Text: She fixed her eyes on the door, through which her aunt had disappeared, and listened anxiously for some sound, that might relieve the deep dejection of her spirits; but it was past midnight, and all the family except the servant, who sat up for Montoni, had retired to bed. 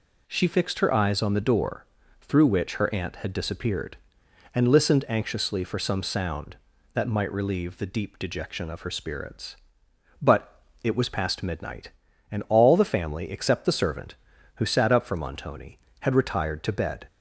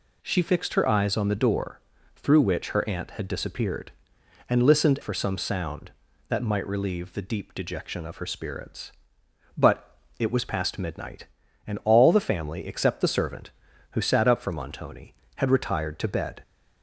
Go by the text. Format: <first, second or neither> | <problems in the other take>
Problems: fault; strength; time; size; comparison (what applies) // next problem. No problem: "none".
first | skips "anxiously"; at 5.0 s // pauses between "but" and "it"; slight; at 9.9 s; 0.20 s long; slight in the first